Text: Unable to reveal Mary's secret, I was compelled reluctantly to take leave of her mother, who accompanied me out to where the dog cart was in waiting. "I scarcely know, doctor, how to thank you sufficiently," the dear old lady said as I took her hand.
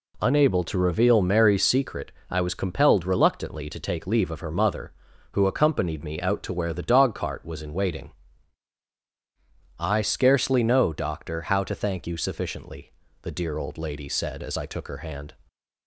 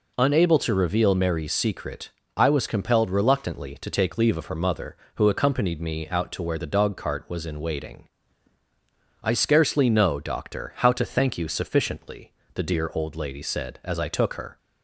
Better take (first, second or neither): first